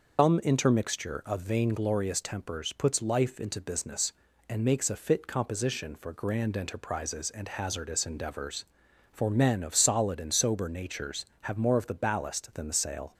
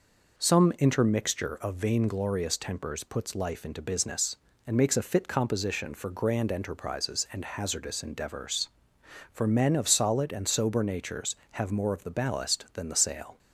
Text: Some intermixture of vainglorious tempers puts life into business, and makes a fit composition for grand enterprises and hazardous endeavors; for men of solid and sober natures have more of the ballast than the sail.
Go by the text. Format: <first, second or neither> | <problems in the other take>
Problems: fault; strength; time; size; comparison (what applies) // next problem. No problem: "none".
second | loses the start of "Some"; at 0.1 s; 135 ms